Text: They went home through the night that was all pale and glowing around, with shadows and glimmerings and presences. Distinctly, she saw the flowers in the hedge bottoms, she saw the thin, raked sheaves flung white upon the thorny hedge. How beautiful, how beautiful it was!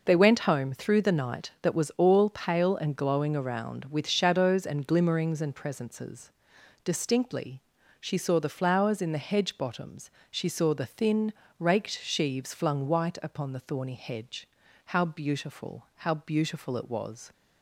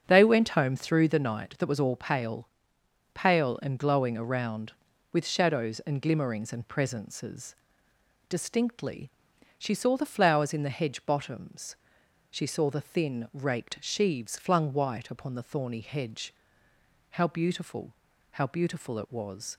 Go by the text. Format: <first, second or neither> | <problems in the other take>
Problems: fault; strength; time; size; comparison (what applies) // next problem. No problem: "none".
first | starts louder than the rest; until 1.0 s; 7 dB // says "pale" twice; at 3.1 s